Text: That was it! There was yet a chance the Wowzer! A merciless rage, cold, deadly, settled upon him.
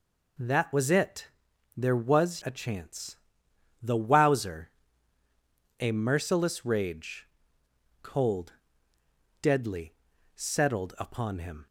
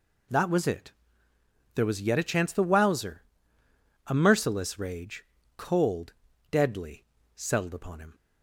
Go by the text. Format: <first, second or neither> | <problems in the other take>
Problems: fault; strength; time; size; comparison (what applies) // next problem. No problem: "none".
second | skips "yet"; at 2.4 s // pauses between "chance" and "the"; noticeable; at 3.1 s; 0.66 s long